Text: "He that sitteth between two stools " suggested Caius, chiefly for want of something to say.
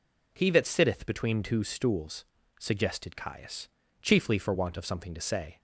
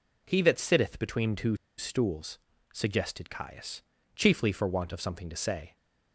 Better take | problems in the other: first | pauses between "two" and "stools"; slight; at 1.5 s; 0.22 s long

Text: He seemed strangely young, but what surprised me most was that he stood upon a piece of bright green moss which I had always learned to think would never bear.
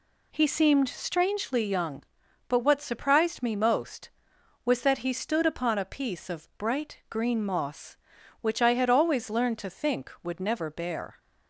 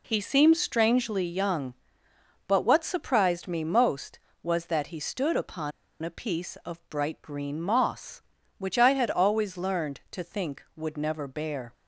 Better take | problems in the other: first | pauses between "upon" and "a"; slight; at 5.7 s; 0.31 s long

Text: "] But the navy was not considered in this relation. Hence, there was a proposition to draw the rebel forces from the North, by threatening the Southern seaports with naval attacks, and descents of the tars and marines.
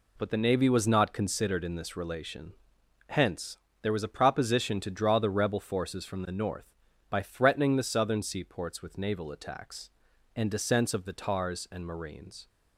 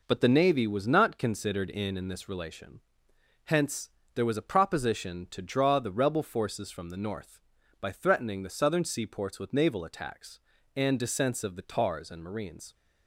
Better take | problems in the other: first | says "in" twice; at 1.9 s

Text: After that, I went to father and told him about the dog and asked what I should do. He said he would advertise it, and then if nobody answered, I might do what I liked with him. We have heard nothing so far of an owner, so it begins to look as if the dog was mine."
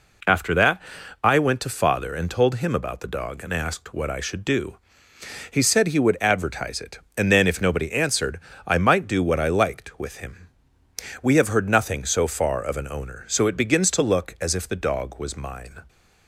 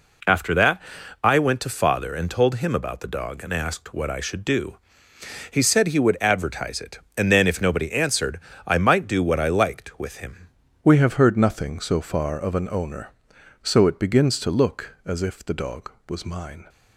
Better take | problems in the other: first | changes voice at "We"; from 10.8 s on; 5.8 s long

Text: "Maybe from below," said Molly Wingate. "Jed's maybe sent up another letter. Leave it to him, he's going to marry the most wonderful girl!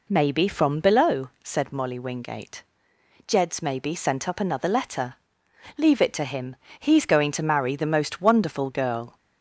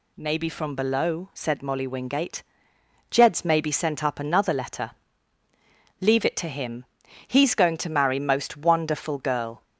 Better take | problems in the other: first | skips "the"; at 8.1 s

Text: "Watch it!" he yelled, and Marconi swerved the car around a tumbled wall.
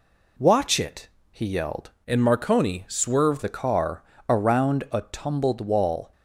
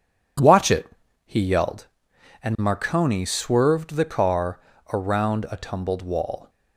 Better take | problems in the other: second | changes voice from "and" to "swerved"; from 2.0 to 3.4 s; 1.4 s long // pauses between "car" and "around"; slight; at 4.0 s; 0.26 s long; slight in the second

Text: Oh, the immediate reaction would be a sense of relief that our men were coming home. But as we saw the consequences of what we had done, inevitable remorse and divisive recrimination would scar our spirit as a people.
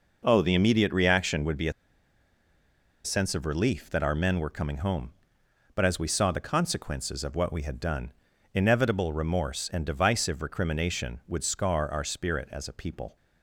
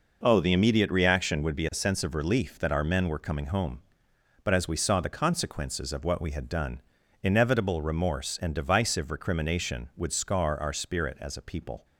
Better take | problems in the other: second | pauses between "a" and "sense"; strong; at 1.7 s; 1.3 s long

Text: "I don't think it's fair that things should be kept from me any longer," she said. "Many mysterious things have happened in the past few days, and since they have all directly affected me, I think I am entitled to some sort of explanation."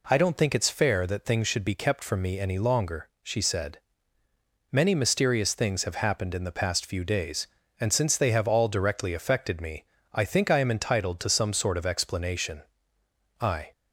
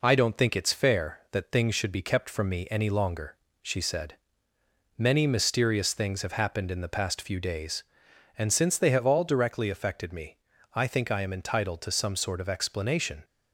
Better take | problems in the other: second | goes on to say "I"; slight; from 13.3 s on; 0.32 s long

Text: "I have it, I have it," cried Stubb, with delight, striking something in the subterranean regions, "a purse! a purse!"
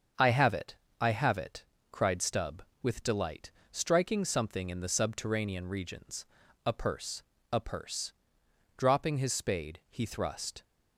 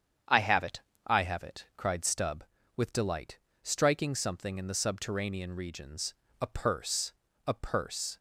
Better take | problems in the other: second | starts louder than the rest; until 1.4 s; 7 dB; strong in the second // goes on to say "Dropping his spade he thrust"; strong; from 8.7 s on; 1.8 s long

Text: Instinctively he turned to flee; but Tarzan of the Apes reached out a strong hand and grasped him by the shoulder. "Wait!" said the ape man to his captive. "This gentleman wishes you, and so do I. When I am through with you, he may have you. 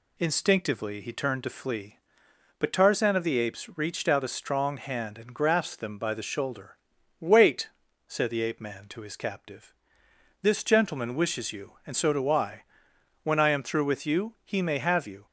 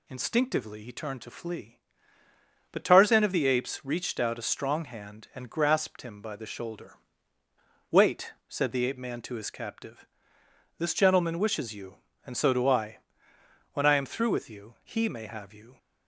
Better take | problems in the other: second | says "them" for "him"; at 5.7 s

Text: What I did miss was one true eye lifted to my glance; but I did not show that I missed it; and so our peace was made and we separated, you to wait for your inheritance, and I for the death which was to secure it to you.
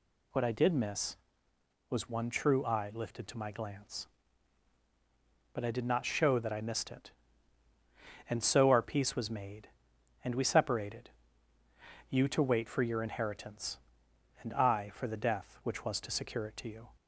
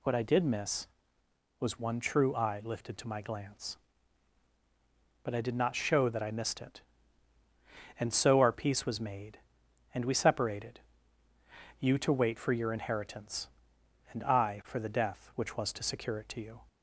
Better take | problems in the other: neither | none

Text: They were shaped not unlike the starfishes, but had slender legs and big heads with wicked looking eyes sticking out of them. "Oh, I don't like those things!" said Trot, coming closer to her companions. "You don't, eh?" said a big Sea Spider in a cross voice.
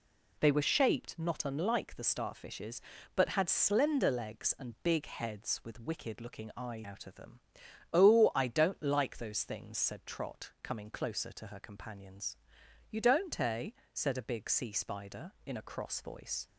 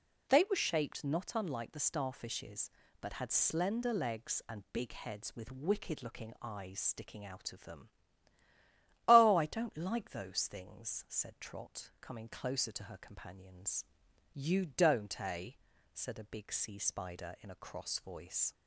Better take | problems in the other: second | skips "sticking"; at 6.8 s

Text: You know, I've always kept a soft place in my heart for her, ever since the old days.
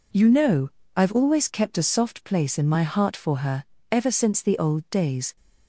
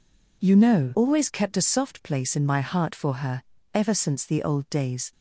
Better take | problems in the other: first | skips "I've"; at 0.9 s

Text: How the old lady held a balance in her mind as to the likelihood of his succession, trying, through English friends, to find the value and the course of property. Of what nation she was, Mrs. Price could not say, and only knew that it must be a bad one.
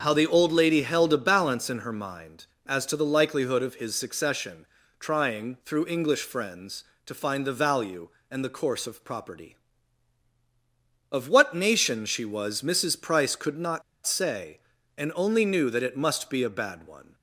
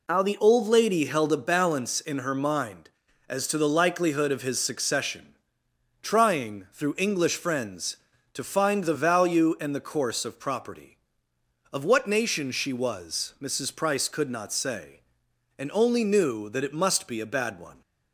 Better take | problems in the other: second | starts louder than the rest; until 1.0 s; 6.5 dB // pauses between "not" and "say"; slight; at 13.8 s; 0.24 s long

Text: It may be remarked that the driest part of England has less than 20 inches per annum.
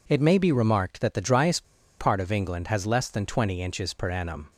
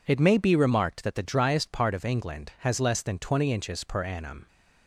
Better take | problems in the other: second | pauses between "driest" and "part"; slight; at 1.6 s; 0.35 s long

